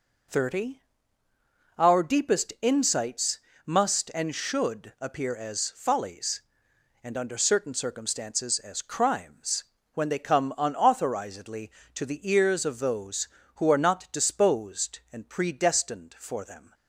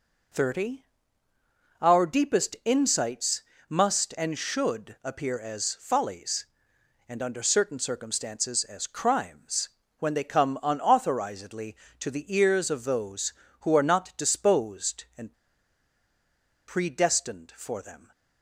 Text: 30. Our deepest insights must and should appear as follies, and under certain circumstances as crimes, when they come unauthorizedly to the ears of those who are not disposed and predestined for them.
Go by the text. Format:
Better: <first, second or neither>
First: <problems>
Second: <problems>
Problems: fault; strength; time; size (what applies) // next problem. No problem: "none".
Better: first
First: pauses between "insights" and "must"; slight; at 3.3 s; 0.26 s long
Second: pauses between "insights" and "must"; slight; at 3.4 s; 0.26 s long // pauses between "and" and "predestined"; strong; at 15.3 s; 1.3 s long